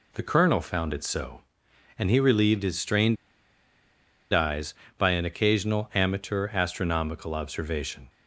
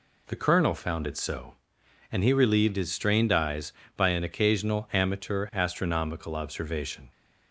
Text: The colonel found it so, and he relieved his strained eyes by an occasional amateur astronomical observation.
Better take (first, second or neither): second